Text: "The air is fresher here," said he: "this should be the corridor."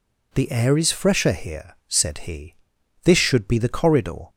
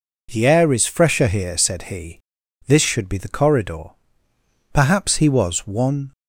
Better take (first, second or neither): first